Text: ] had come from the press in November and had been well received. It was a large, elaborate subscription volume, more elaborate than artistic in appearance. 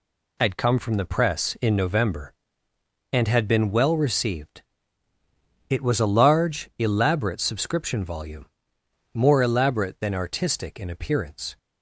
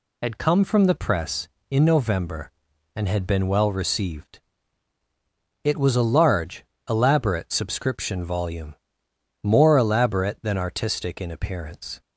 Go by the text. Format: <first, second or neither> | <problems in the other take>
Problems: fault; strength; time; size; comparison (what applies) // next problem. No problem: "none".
neither | none